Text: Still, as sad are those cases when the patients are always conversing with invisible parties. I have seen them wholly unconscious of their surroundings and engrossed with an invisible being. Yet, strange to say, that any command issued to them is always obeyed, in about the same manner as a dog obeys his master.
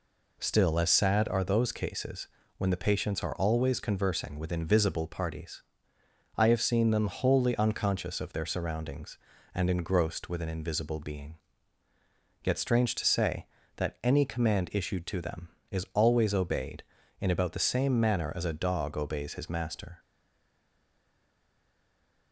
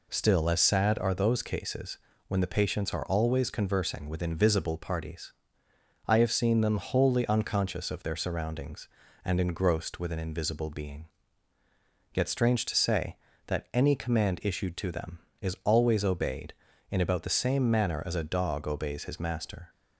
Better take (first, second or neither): second